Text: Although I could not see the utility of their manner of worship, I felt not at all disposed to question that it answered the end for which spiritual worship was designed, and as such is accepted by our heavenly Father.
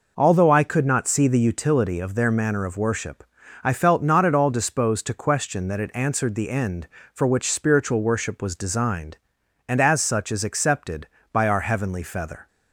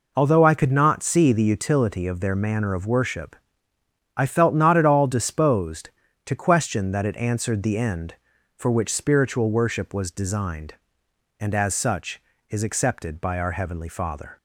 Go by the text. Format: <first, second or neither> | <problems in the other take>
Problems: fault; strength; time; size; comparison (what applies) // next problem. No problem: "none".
second | says "Feather" for "Father"; at 12.0 s